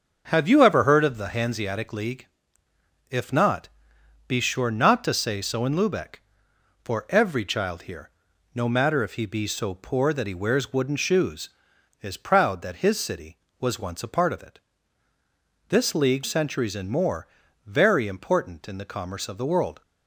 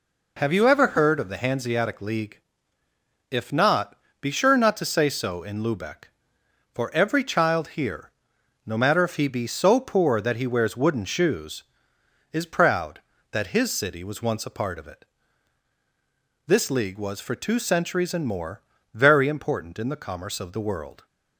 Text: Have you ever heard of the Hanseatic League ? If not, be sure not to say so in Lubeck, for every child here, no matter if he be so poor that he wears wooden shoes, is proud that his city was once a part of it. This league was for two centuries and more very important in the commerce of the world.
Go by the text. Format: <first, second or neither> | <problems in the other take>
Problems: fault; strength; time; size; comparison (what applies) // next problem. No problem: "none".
second | starts louder than the rest; until 1.3 s; 6.5 dB // skips "was for two"; at 16.2 s // pauses between "more" and "very"; at 17.2 s; 0.40 s long; slight in the second